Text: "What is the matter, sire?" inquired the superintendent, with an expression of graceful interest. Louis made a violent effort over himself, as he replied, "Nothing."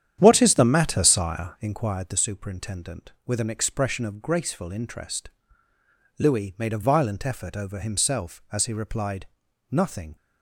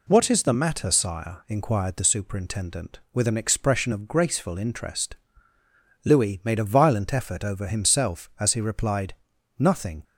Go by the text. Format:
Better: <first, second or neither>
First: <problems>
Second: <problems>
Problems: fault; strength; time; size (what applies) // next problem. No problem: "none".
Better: second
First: starts louder than the rest; strong; until 1.8 s; 9.5 dB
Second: none